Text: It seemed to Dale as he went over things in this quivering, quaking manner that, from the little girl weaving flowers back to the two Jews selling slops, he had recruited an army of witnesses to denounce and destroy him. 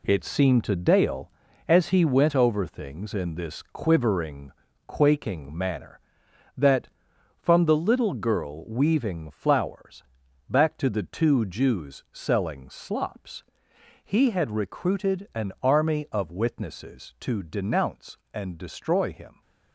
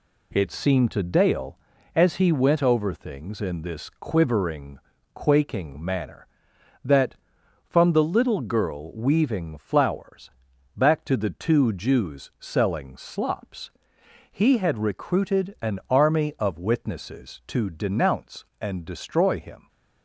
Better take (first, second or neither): second